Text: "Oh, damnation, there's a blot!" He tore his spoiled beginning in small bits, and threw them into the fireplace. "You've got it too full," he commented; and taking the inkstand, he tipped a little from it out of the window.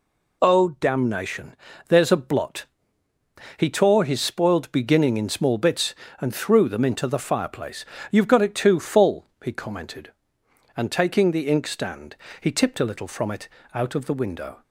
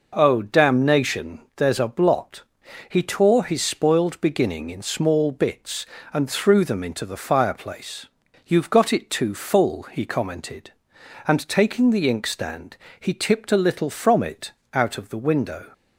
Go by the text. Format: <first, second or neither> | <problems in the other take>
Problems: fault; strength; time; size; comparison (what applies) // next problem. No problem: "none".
neither | pauses between "it" and "out"; slight; the same in both